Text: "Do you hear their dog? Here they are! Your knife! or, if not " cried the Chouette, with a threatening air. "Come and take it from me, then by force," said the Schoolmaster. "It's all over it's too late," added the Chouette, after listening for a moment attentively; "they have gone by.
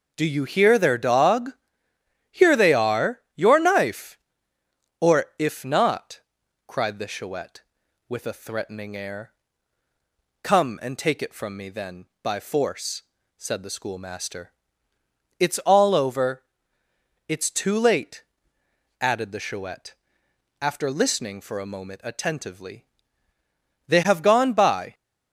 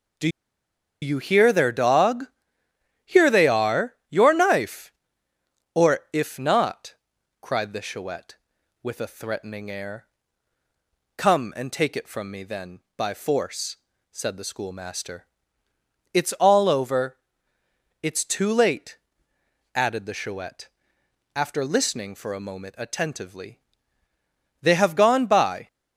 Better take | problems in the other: first | pauses between "Do" and "you"; noticeable; at 0.2 s; 0.73 s long // pauses between "over" and "it's"; noticeable; at 17.1 s; 0.84 s long; noticeable in the first

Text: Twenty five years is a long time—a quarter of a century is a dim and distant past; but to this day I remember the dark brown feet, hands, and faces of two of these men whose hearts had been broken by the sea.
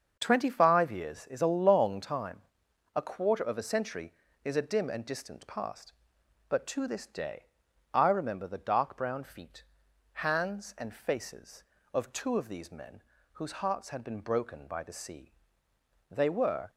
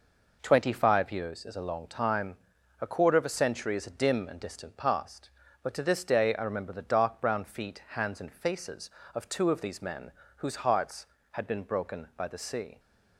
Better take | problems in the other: second | starts louder than the rest; until 1.2 s; 6.5 dB // pauses between "day" and "I"; noticeable; at 7.4 s; 0.48 s long // pauses between "men" and "whose"; slight; at 13.0 s; 0.32 s long; slight in the second // goes on to say "They were"; from 16.0 s on; 0.60 s long

